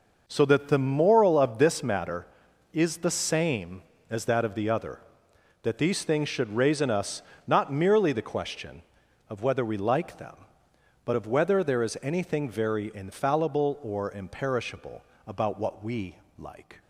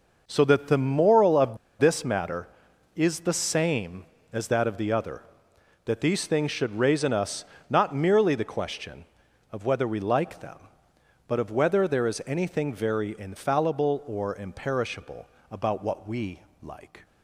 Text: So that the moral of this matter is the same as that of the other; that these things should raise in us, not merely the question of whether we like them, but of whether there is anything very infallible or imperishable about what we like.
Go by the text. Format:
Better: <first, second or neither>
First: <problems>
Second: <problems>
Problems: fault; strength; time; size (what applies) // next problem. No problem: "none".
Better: first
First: pauses between "imperishable" and "about"; slight; at 15.0 s; 0.24 s long // pauses between "we" and "like"; slight; at 16.1 s; 0.22 s long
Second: pauses between "of" and "this"; slight; at 1.5 s; 0.22 s long // pauses between "imperishable" and "about"; slight; at 15.2 s; 0.24 s long // pauses between "we" and "like"; slight; at 16.4 s; 0.22 s long